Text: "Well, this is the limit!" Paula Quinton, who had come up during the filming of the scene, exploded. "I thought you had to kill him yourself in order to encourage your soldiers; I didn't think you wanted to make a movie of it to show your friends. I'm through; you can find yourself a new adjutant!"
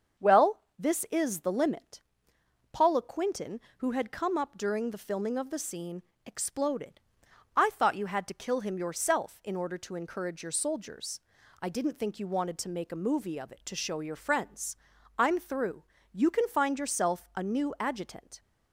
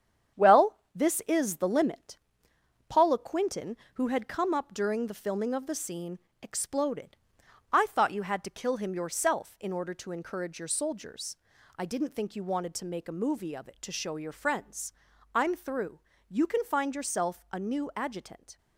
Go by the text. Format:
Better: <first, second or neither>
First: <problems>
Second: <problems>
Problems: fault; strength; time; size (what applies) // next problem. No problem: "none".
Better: first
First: starts louder than the rest; until 1.4 s; 7 dB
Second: gets quieter; throughout; 6 dB // starts louder than the rest; strong; until 1.5 s; 8.5 dB